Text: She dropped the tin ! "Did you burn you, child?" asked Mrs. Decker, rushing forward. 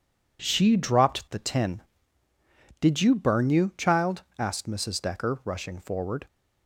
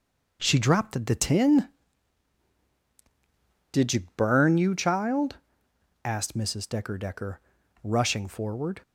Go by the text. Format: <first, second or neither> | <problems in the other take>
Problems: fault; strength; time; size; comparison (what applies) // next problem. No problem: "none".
first | says "Decker" twice; at 6.9 s